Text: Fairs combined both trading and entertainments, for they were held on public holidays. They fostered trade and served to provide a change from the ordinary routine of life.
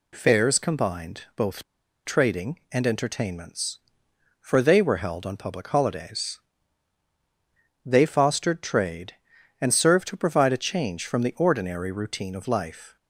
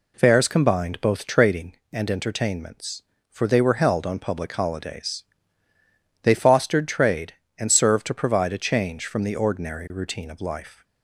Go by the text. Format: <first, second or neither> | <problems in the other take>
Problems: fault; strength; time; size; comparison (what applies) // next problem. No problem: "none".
second | pauses between "both" and "trading"; at 1.6 s; 0.42 s long